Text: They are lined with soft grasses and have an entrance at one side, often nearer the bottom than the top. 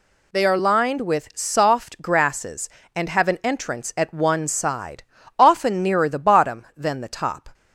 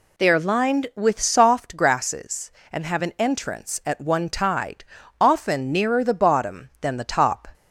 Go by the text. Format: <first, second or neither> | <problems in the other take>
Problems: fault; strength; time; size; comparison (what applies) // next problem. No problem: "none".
first | says "tide" for "side"; at 4.2 s